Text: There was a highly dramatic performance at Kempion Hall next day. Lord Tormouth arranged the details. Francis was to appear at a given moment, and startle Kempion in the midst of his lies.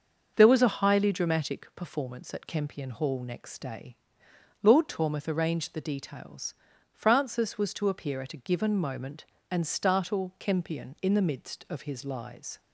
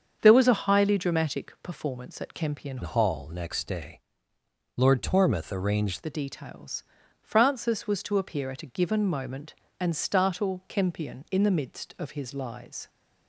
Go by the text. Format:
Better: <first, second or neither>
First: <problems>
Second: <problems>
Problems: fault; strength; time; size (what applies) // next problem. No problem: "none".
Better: first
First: starts louder than the rest; until 1.3 s; 6.5 dB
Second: starts louder than the rest; strong; until 1.2 s; 7 dB // changes voice from "Hall" to "arranged"; from 2.8 to 6.0 s; 3.2 s long